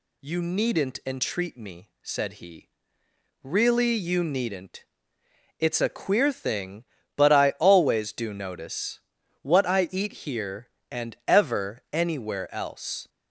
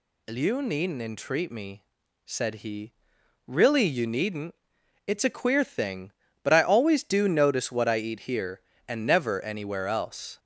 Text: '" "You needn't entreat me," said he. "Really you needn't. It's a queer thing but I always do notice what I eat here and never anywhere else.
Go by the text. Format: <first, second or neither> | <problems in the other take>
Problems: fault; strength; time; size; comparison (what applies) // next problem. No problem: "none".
second | pauses between "notice" and "what"; at 9.0 s; 0.40 s long // pauses between "eat" and "here"; slight; at 10.1 s; 0.16 s long // says "ever" for "never"; at 11.2 s